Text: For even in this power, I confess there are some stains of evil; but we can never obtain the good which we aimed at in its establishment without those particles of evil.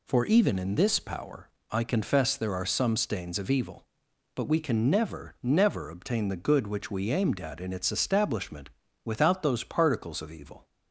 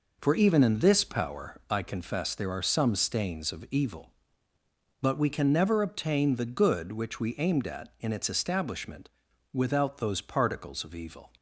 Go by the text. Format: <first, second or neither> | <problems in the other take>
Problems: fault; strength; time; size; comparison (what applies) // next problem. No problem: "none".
second | says "never" twice; at 5.4 s // pauses between "establishment" and "without"; slight; at 8.6 s; 0.36 s long; also in the second